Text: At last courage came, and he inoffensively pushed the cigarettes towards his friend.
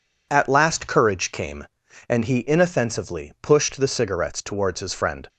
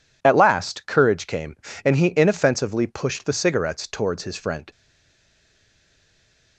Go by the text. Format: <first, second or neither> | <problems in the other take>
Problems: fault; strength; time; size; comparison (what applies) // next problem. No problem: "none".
first | stays silent after the last word; noticeable; from 4.7 s on; 1.8 s long